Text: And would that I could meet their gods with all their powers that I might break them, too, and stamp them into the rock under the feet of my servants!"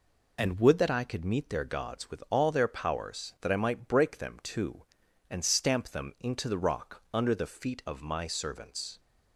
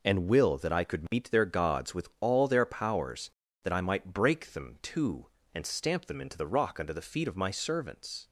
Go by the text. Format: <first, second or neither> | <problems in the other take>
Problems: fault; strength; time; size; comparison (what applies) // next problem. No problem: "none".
first | says "will" for "would"; at 0.2 s